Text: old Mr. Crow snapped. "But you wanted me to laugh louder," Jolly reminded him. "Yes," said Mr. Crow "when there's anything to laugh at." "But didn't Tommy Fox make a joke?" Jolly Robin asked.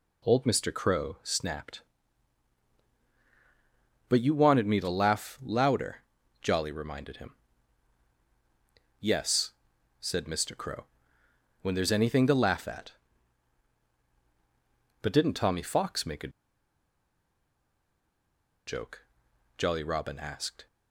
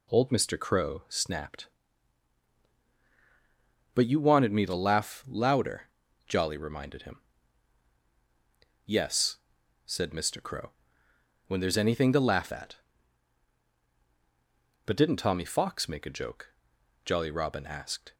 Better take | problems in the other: second | pauses between "Crow" and "when"; noticeable; at 10.8 s; 0.76 s long; noticeable in the second // pauses between "a" and "joke"; strong; at 16.3 s; 2.3 s long

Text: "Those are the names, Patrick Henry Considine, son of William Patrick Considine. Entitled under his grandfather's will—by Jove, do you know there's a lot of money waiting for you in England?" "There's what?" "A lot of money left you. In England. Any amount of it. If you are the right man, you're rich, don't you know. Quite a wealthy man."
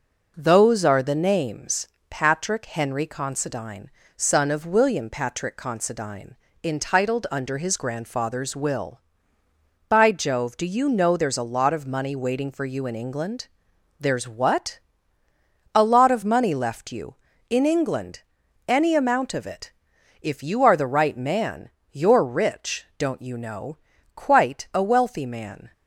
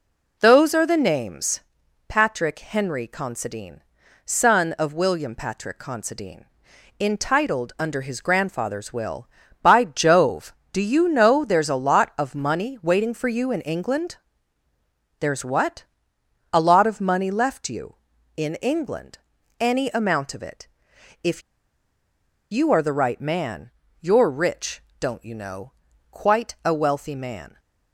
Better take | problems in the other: first | pauses between "If" and "you"; at 21.4 s; 1.0 s long

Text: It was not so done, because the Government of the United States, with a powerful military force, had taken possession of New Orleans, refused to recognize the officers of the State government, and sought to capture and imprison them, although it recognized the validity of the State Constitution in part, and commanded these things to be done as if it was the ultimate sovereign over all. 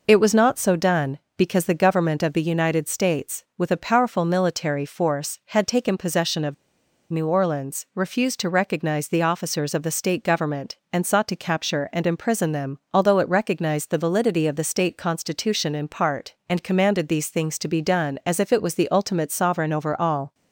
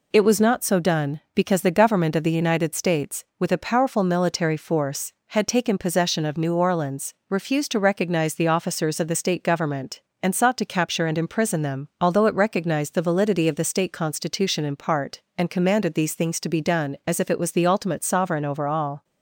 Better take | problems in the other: second | pauses between "of" and "New"; noticeable; at 6.5 s; 0.55 s long

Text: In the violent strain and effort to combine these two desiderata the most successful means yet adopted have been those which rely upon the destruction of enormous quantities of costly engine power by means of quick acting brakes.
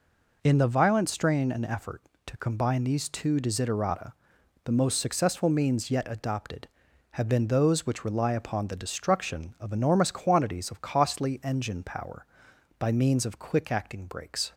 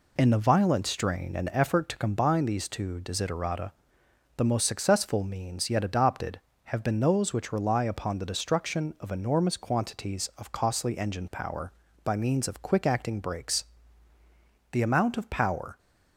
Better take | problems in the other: first | pauses between "desiderata" and "the"; noticeable; at 3.7 s; 0.66 s long; noticeable in the first // goes on to say "The amount of power"; noticeable; from 14.7 s on; 1.0 s long

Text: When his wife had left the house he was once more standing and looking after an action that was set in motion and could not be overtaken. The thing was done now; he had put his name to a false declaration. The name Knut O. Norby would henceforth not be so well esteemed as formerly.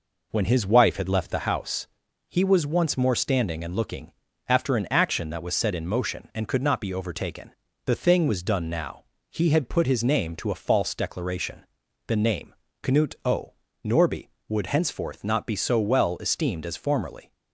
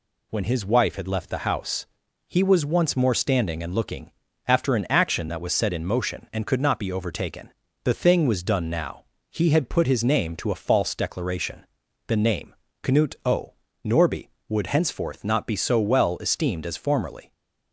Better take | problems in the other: second | starts louder than the rest; noticeable; until 1.6 s; 4.5 dB // pauses between "house" and "he"; at 1.8 s; 0.40 s long; also in the second // pauses between "looking" and "after"; slight; at 4.1 s; 0.36 s long; slight in the second // pauses between "name" and "Knut"; slight; at 12.5 s; 0.28 s long; slight in the second

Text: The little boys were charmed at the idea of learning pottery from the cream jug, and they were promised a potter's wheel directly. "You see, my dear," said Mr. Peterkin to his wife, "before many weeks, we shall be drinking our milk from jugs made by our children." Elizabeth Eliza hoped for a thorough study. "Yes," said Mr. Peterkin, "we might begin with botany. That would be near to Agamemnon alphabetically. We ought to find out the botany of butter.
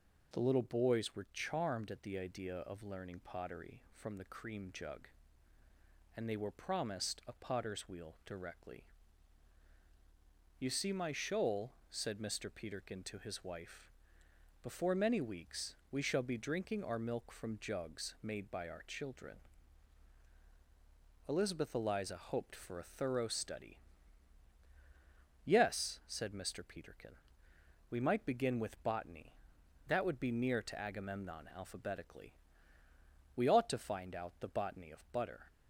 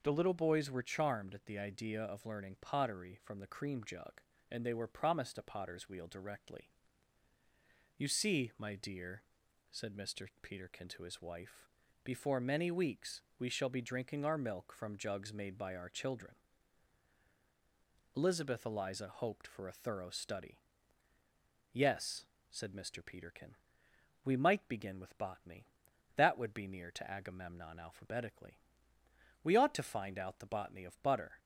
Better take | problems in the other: second | says "shoal" for "dear"; at 11.1 s

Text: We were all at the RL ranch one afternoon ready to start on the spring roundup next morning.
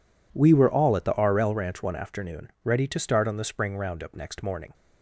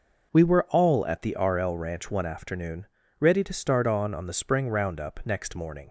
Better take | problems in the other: first | pauses between "afternoon" and "ready"; slight; at 2.8 s; 0.34 s long // says "on" twice; at 4.1 s

